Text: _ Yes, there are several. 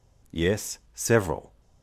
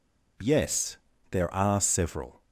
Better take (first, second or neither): second